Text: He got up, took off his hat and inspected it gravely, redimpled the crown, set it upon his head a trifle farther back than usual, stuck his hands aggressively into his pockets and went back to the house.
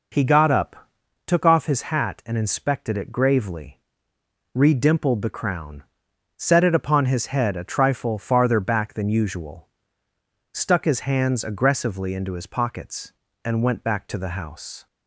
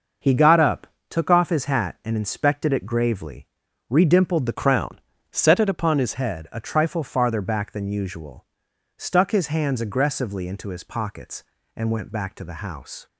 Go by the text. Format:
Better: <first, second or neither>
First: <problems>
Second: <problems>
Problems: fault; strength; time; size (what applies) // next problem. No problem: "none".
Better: first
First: none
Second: starts louder than the rest; noticeable; until 1.4 s; 6 dB // changes voice from "crown" to "his"; from 4.5 to 6.1 s; 1.6 s long